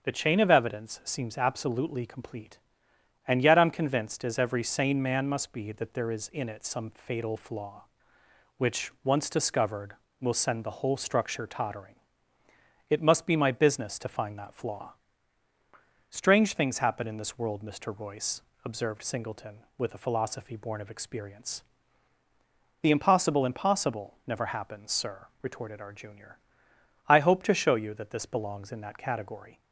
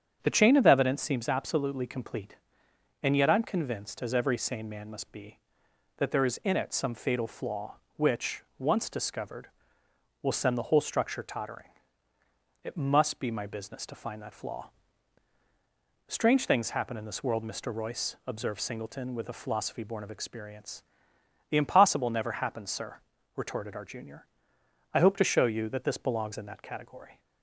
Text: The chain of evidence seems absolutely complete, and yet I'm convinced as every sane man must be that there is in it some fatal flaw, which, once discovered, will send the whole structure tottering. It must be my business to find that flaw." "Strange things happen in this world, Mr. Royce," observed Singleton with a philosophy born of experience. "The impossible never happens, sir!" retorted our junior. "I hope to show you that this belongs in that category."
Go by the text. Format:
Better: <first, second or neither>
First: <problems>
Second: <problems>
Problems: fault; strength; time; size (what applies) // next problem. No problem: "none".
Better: second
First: starts louder than the rest; until 1.0 s; 7 dB // says "impossible" twice; at 23.4 s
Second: starts louder than the rest; strong; until 1.2 s; 8 dB